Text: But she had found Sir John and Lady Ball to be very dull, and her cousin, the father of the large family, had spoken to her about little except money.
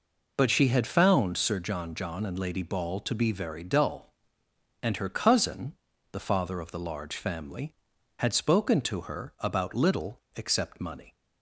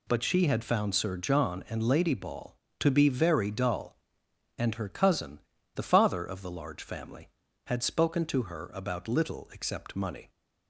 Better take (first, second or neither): second